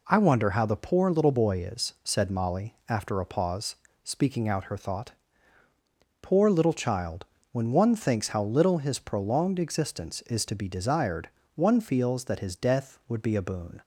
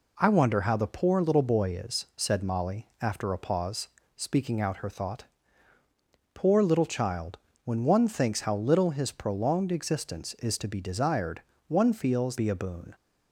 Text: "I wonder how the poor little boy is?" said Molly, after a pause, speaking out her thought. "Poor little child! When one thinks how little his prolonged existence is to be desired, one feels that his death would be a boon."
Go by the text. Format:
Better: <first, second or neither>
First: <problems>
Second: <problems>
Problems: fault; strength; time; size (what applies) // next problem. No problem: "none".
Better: first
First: none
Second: skips "that his death would"; at 12.3 s